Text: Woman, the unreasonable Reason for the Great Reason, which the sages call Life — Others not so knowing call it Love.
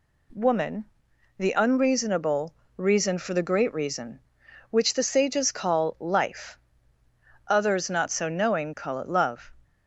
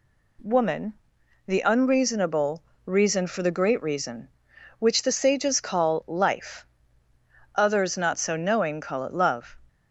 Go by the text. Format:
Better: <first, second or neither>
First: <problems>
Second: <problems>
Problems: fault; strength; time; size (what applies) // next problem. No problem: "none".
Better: neither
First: pauses between "unreasonable" and "Reason"; slight; at 2.5 s; 0.22 s long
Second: pauses between "unreasonable" and "Reason"; slight; at 2.6 s; 0.22 s long